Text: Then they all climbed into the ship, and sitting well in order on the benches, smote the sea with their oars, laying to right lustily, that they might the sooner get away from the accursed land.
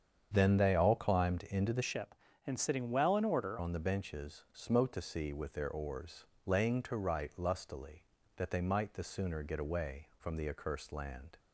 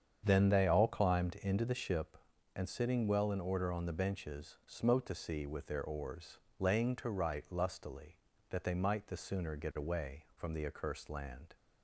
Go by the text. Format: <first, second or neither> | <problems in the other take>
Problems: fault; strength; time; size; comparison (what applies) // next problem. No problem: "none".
second | starts louder than the rest; strong; until 1.3 s; 8 dB; strong in the second // changes voice from "ship" to "order"; from 1.8 to 3.5 s; 1.7 s long